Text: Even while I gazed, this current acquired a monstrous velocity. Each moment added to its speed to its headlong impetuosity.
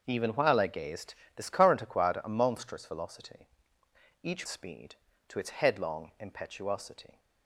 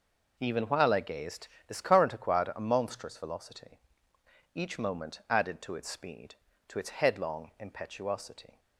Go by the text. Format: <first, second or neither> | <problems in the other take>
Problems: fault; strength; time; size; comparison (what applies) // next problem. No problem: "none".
second | starts louder than the rest; until 1.0 s; 6.5 dB // skips "moment added to its"; at 4.4 s